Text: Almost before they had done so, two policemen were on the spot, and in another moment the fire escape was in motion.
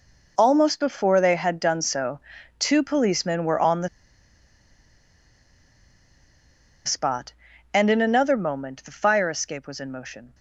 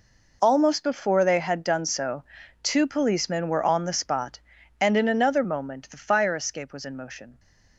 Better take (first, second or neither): second